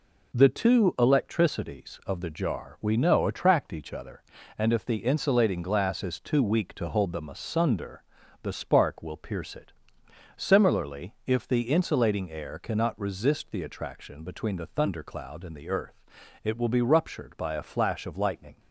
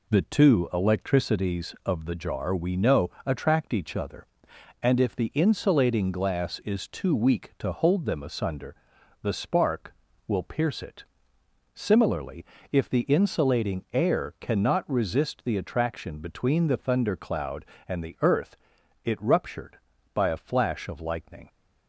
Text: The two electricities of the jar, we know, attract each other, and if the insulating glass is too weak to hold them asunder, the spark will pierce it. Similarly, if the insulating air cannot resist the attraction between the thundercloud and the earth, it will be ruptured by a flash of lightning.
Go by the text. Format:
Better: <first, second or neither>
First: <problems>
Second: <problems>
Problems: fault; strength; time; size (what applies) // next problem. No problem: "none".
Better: first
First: none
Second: skips "will be"; at 19.1 s